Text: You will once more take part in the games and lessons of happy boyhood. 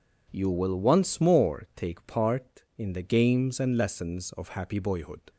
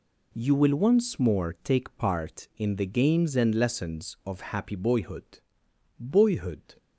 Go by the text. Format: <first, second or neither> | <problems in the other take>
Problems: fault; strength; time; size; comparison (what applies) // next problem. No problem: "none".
first | says "boyhood" twice; at 5.9 s